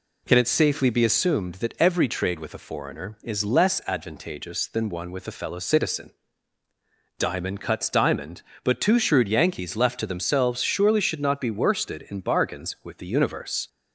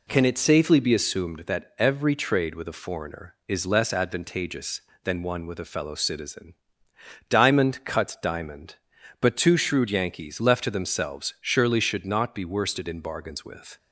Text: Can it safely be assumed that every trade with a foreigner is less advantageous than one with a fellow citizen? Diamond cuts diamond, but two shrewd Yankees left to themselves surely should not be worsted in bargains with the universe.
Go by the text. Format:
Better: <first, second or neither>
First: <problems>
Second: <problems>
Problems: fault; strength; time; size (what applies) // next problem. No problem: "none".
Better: first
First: none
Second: stops before "the universe"; at 13.7 s